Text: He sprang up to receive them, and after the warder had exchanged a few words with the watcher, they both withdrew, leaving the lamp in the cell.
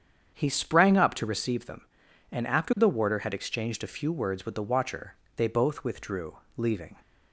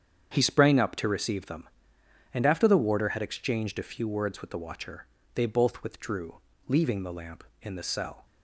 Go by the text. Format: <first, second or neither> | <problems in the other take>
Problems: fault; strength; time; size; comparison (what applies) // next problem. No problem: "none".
second | starts louder than the rest; strong; until 1.3 s; 8 dB; strong in the second // stops before "the lamp in the cell"; at 7.0 s